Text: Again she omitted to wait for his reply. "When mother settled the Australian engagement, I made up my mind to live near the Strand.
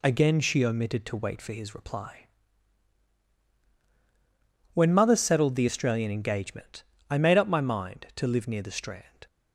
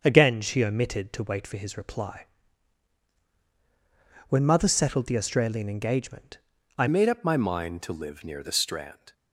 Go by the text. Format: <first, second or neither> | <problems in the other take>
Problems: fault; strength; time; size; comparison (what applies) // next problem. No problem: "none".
first | starts louder than the rest; until 1.0 s; 6.5 dB // changes voice at "made"; from 6.8 s on; 2.3 s long